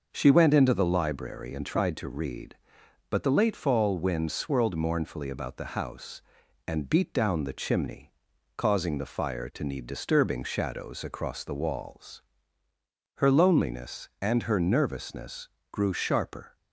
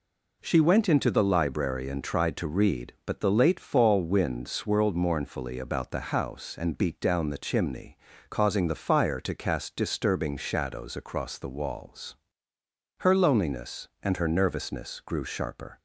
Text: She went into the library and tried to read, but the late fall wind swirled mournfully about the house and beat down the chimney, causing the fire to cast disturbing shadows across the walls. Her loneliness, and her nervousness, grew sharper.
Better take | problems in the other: second | says "need" for "cast"; at 9.6 s

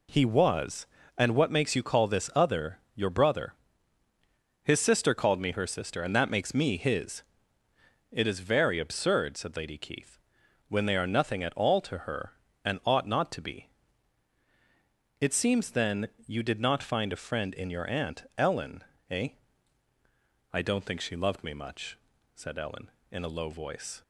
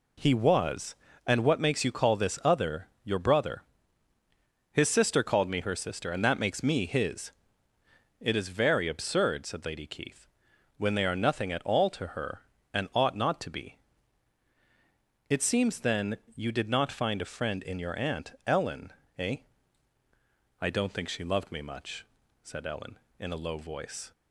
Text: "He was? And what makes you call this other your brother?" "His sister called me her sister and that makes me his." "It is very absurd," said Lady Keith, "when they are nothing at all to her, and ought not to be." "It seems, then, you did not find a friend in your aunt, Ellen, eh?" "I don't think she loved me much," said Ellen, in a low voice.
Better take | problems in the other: neither | pauses between "other" and "your"; slight; the same in both

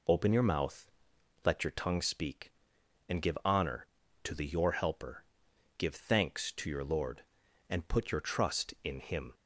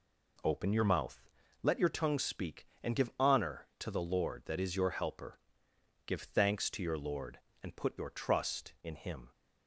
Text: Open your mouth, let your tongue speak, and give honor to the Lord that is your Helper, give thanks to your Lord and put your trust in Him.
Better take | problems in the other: second | skips "Lord that is"; at 4.4 s

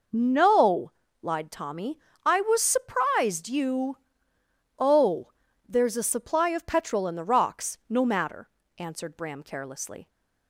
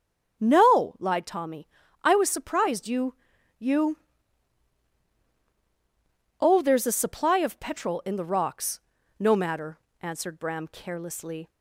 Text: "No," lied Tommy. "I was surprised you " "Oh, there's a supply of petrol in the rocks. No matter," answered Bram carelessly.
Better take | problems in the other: first | starts louder than the rest; strong; until 1.4 s; 7 dB // says "you" twice; at 3.5 s

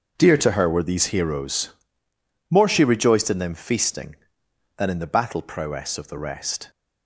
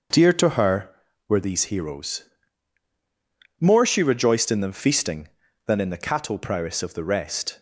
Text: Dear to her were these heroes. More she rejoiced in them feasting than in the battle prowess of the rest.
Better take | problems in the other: first | starts louder than the rest; noticeable; until 1.5 s; 6 dB; also in the first // says "cattle" for "battle"; at 6.0 s

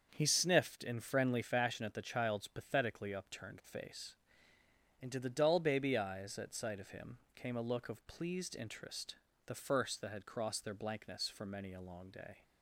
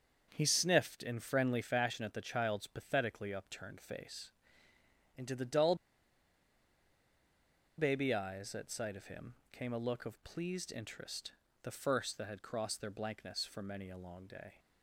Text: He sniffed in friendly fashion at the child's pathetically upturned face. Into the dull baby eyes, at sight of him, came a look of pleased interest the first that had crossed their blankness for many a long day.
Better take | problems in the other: first | starts louder than the rest; until 1.3 s; 6.5 dB; also in the first // pauses between "dull" and "baby"; strong; at 5.7 s; 2.0 s long // pauses between "interest" and "the"; slight; at 11.3 s; 0.30 s long; slight in the first

